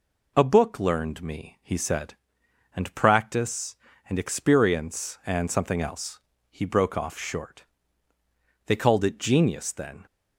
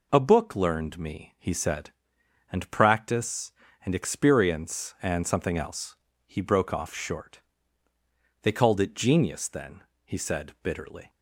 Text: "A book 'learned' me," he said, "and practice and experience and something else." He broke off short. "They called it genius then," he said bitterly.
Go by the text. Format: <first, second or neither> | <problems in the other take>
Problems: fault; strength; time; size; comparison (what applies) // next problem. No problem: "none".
second | stops before "he said bitterly"; at 10.0 s